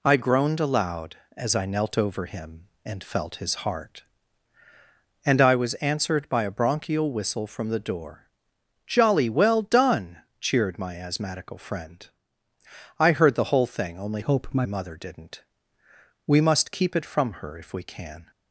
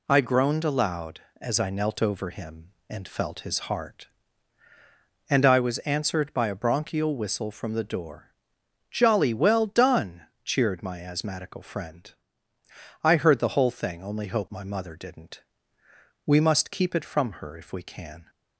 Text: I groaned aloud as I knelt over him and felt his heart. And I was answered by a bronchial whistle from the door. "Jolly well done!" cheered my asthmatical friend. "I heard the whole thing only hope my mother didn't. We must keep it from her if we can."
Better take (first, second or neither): second